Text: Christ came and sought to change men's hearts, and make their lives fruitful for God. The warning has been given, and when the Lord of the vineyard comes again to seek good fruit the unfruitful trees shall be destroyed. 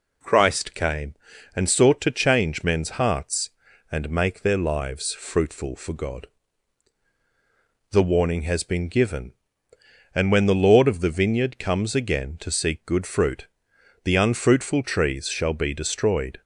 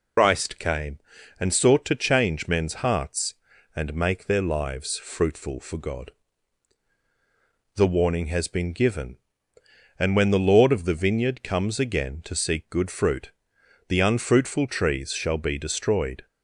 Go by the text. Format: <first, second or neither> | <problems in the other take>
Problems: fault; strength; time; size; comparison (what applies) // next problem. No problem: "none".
first | loses the start of "Christ"; at 0.1 s; 115 ms // pauses between "fruit" and "the"; noticeable; at 13.3 s; 0.56 s long; noticeable in the first